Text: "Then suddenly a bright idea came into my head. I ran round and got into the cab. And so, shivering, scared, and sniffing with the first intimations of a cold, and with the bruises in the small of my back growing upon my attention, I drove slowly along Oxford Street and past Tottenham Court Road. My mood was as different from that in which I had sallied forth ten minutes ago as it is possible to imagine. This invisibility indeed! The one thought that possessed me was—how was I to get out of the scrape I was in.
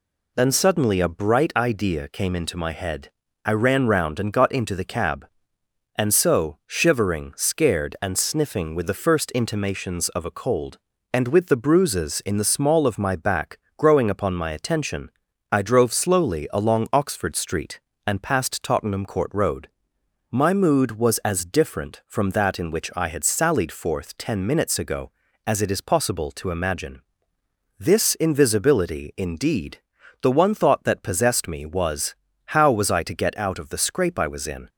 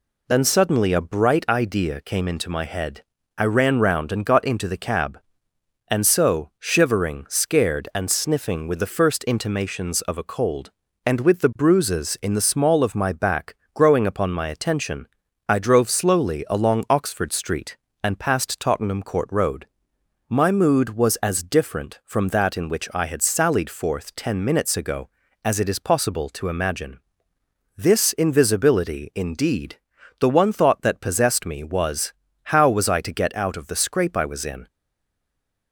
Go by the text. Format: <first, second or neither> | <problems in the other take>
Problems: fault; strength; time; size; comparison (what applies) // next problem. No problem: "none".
first | pauses between "back" and "growing"; slight; at 13.5 s; 0.20 s long; slight in the first // stays silent after the last word; from 34.6 s on; 1.1 s long